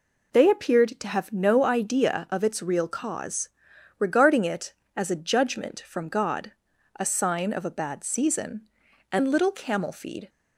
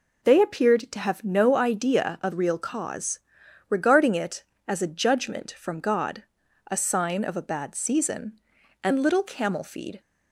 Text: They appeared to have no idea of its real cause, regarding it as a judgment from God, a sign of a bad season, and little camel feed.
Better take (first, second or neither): first